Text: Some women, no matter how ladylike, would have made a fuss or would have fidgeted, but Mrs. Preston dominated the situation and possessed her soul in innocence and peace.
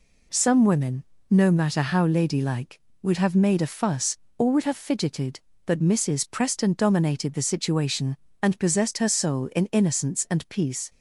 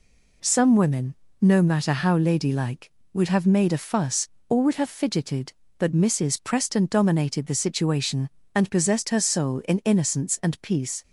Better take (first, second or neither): neither